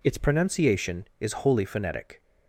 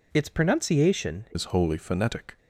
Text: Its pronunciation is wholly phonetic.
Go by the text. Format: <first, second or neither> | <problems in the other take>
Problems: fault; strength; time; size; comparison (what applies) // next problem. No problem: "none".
first | changes voice at "is"; from 1.3 s on; 1.0 s long